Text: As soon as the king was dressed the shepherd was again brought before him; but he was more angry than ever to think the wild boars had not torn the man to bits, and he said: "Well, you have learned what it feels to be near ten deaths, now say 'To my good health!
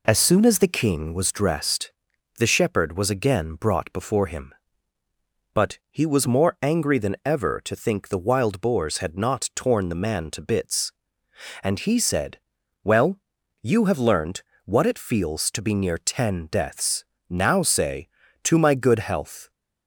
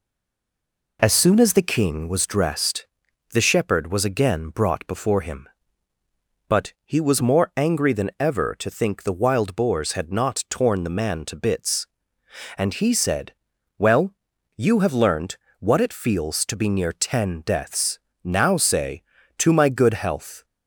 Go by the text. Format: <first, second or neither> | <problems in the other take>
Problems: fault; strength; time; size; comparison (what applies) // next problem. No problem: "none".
first | stays silent before the first word; until 0.9 s; 0.9 s long // pauses between "dressed" and "the"; noticeable; at 2.8 s; 0.48 s long; noticeable in the first // pauses between "learned" and "what"; slight; at 15.3 s; 0.22 s long; slight in the first